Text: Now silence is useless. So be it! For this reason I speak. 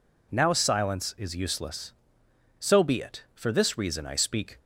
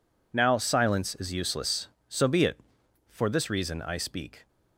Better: neither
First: none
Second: none

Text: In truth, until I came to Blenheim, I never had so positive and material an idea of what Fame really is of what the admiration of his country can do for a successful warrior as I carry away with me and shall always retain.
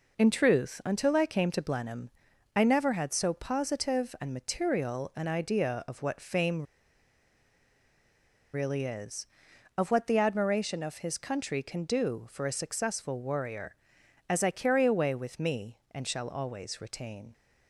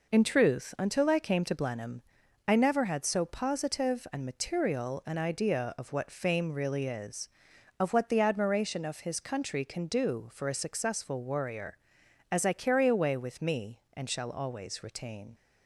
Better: second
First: pauses between "Fame" and "really"; strong; at 6.6 s; 1.9 s long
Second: none

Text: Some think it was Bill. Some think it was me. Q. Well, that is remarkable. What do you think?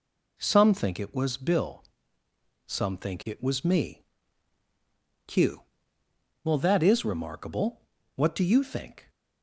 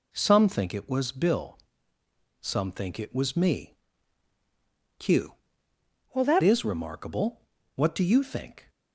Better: first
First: none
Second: changes voice from "Well" to "that"; from 6.1 to 6.4 s; 0.3 s long

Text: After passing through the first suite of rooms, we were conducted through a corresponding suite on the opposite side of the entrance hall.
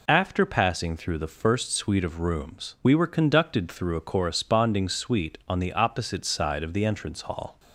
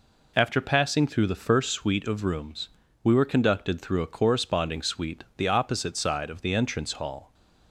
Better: first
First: none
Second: skips "on"; at 5.3 s

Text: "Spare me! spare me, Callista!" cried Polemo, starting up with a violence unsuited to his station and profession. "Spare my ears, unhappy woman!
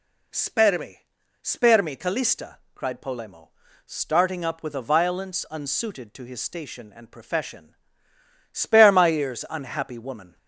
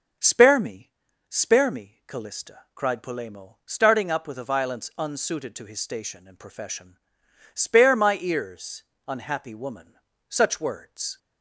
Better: first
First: none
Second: goes on to say "such words"; noticeable; from 10.3 s on; 0.88 s long

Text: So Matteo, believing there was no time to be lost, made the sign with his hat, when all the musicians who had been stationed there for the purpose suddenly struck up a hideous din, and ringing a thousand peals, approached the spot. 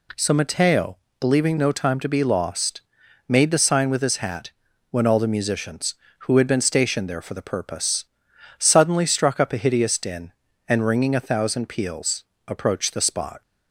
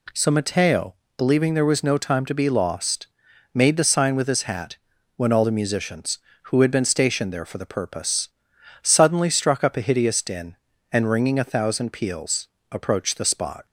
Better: second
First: skips "there was"; at 1.5 s // pauses between "purpose" and "suddenly"; noticeable; at 8.0 s; 0.54 s long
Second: pauses between "purpose" and "suddenly"; noticeable; at 8.2 s; 0.54 s long

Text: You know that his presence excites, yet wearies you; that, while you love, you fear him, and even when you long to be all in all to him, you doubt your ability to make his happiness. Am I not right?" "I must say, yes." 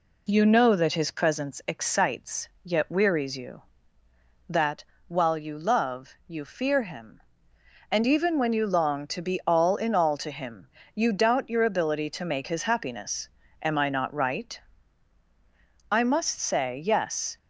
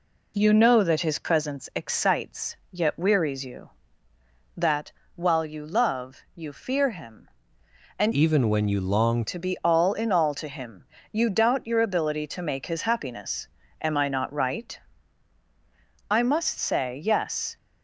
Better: first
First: none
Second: changes voice from "even" to "long"; from 8.1 to 9.2 s; 1.1 s long

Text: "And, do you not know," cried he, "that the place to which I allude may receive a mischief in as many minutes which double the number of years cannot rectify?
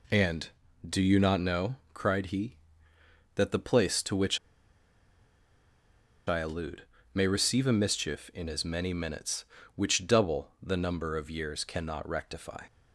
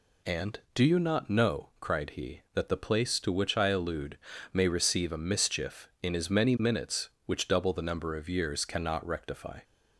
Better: second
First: pauses between "which" and "I"; strong; at 4.3 s; 1.9 s long // pauses between "allude" and "may"; slight; at 6.8 s; 0.32 s long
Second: pauses between "allude" and "may"; slight; at 4.1 s; 0.34 s long

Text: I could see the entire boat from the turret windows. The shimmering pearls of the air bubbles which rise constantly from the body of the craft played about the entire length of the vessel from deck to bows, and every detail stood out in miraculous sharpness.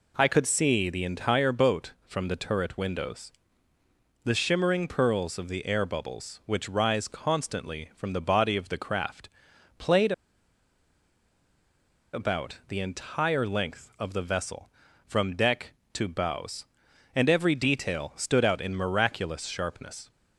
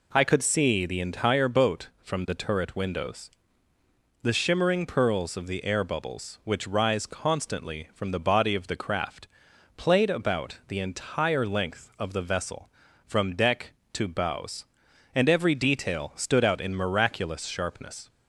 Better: second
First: pauses between "craft" and "played"; noticeable; at 9.2 s; 0.50 s long // pauses between "played" and "about"; strong; at 10.1 s; 2.0 s long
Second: pauses between "craft" and "played"; noticeable; at 9.2 s; 0.50 s long

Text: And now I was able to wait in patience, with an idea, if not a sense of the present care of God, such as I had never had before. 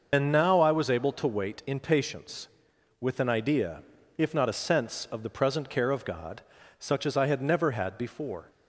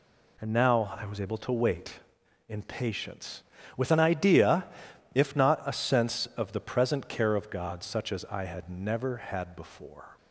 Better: second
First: loses the start of "And"; at 0.1 s; 65 ms // starts louder than the rest; noticeable; until 1.1 s; 6 dB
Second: none

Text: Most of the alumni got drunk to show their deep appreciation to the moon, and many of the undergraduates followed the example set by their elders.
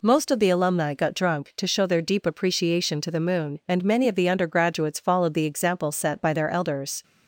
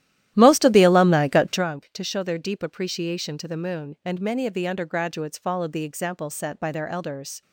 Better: first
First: none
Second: starts louder than the rest; strong; until 1.7 s; 13 dB

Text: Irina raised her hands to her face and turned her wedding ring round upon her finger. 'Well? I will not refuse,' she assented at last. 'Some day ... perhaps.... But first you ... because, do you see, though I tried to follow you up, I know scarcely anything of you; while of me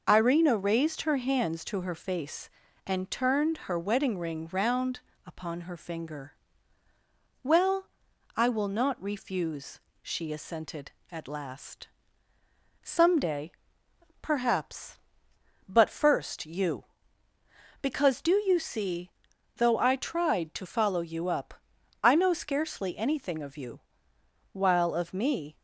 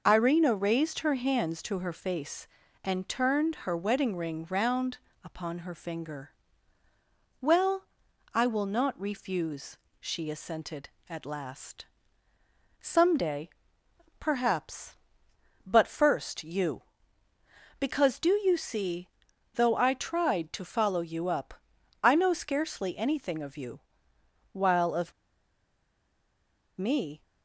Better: first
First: pauses between "round" and "upon"; slight; at 4.9 s; 0.26 s long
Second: pauses between "round" and "upon"; slight; at 4.9 s; 0.26 s long // pauses between "of" and "me"; strong; at 25.1 s; 1.6 s long

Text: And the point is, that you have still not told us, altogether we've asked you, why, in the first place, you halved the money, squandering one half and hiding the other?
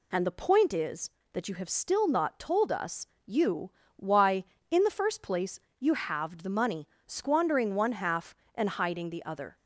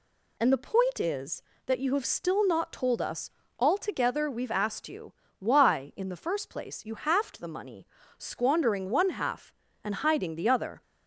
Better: second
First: skips "altogether we've asked"; at 3.1 s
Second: none

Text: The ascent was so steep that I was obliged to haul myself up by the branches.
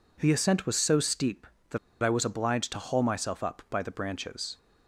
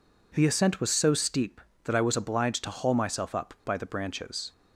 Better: second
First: pauses between "that" and "I"; slight; at 1.7 s; 0.25 s long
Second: none

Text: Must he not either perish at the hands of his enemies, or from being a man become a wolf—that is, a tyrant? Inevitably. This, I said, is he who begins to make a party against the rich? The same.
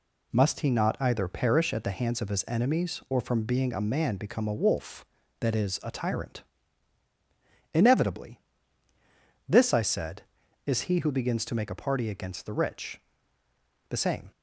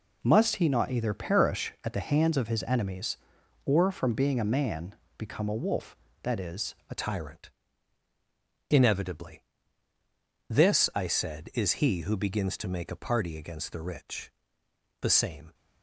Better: first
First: none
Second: pauses between "man" and "become"; slight; at 4.9 s; 0.22 s long // changes voice at "tyrant"; from 6.9 s on; 8.6 s long

